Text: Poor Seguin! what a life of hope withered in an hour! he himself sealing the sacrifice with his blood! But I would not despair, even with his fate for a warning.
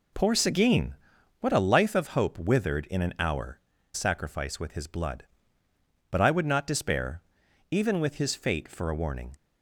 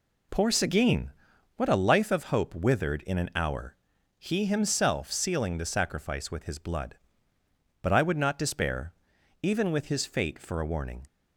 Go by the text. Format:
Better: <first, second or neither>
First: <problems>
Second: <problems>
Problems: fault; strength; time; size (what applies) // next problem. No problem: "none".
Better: second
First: skips "he himself sealing the"; at 3.7 s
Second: none